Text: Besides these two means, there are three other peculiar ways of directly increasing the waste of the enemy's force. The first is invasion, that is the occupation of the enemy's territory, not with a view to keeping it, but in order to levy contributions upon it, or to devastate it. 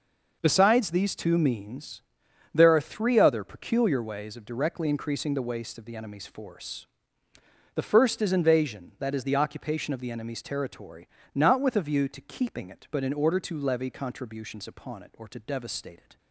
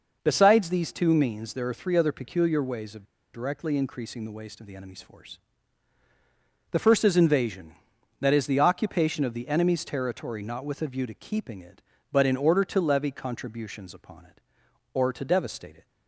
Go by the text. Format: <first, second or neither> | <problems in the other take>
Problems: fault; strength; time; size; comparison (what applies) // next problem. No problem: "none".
first | pauses between "of" and "directly"; slight; at 3.0 s; 0.27 s long